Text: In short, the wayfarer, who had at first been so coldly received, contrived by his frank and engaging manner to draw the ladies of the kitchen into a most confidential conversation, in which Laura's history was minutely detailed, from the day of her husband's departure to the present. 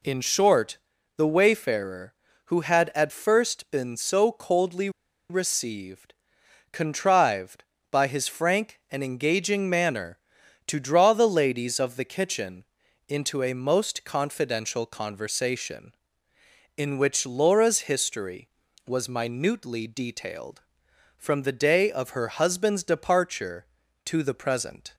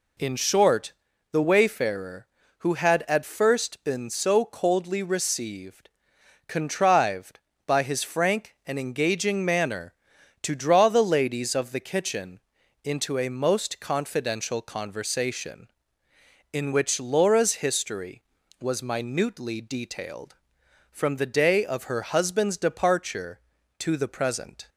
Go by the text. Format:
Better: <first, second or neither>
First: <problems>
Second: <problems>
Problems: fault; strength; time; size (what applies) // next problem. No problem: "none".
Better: second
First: pauses between "coldly" and "received"; at 4.8 s; 0.40 s long // pauses between "kitchen" and "into"; at 12.6 s; 0.42 s long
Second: pauses between "kitchen" and "into"; at 12.4 s; 0.42 s long